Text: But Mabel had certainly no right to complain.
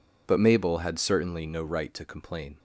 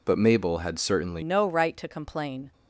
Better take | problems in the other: first | changes voice at "no"; from 1.2 s on; 1.3 s long

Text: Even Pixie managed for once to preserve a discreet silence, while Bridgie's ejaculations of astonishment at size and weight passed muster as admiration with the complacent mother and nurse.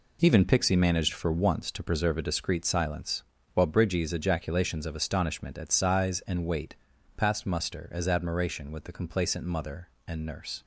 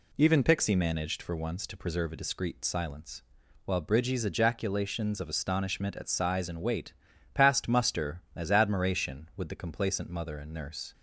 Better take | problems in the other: neither | pauses between "weight" and "passed"; the same in both

